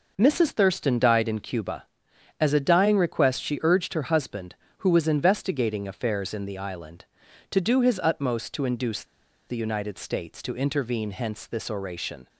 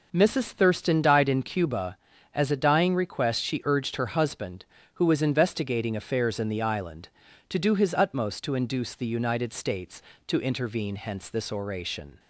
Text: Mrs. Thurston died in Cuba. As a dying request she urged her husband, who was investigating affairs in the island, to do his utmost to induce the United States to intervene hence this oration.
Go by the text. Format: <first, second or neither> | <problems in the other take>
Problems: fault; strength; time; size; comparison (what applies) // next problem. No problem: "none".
second | pauses between "induce" and "the"; at 9.0 s; 0.43 s long